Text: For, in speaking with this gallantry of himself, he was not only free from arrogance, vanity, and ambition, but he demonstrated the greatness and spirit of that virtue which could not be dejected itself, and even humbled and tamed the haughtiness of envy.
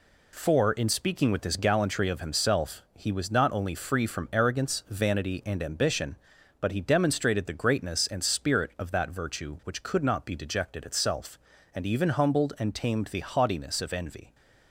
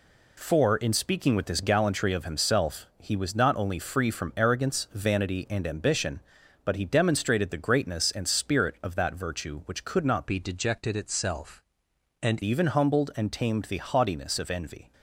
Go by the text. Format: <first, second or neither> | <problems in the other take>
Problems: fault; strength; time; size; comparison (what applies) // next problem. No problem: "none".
first | changes voice from "be" to "and"; from 10.2 to 12.4 s; 2.2 s long